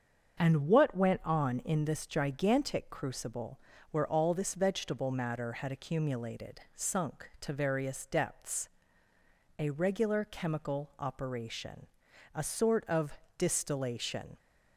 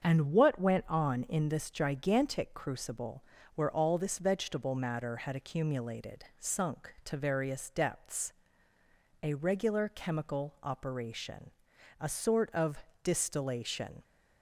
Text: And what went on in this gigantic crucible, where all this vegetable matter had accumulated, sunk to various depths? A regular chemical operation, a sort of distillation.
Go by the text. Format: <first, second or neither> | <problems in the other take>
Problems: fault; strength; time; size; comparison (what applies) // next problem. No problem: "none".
neither | starts louder than the rest; the same in both // pauses between "of" and "distillation"; slight; the same in both